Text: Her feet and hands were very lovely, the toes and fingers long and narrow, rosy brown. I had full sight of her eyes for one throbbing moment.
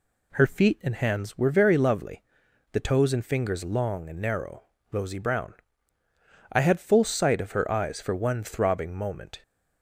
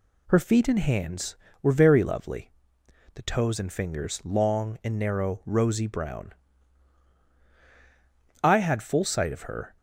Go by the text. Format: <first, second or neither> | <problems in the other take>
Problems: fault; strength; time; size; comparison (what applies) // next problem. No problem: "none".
first | stops before "eyes for one throbbing moment"; at 9.7 s